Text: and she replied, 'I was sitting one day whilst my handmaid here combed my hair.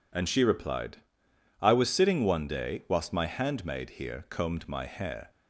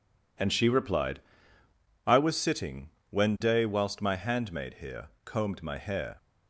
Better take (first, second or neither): first